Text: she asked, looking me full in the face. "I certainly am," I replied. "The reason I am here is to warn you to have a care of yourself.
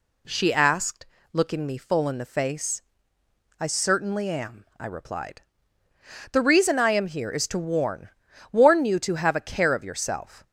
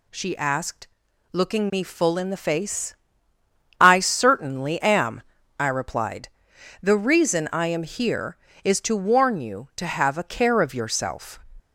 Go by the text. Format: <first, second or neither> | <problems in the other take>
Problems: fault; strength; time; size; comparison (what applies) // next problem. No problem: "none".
second | says "warn" twice; at 8.5 s